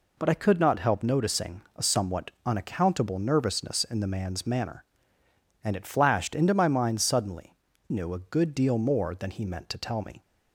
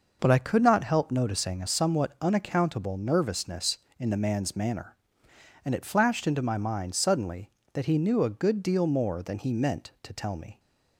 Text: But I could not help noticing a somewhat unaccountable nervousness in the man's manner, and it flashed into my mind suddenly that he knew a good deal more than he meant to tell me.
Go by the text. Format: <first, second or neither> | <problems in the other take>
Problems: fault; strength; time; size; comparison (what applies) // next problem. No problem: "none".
second | pauses between "noticing" and "a"; slight; at 1.6 s; 0.16 s long // skips "that he"; at 7.7 s